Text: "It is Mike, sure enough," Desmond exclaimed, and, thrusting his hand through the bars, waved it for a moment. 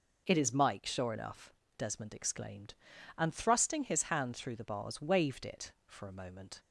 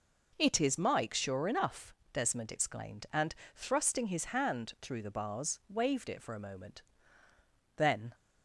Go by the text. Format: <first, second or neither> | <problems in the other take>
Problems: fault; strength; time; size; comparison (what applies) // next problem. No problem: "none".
first | goes on to say "Then"; slight; from 7.7 s on; 0.38 s long